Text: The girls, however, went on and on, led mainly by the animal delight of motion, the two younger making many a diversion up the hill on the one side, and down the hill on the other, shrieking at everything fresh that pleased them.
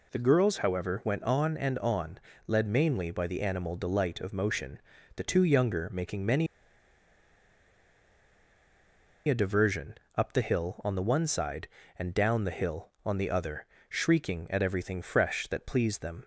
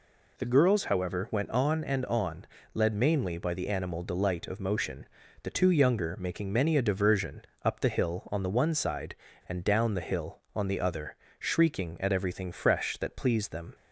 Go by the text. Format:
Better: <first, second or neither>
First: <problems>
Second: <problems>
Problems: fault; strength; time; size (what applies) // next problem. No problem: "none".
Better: second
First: pauses between "many" and "a"; strong; at 6.4 s; 2.8 s long // pauses between "diversion" and "up"; slight; at 9.9 s; 0.22 s long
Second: pauses between "diversion" and "up"; slight; at 7.4 s; 0.22 s long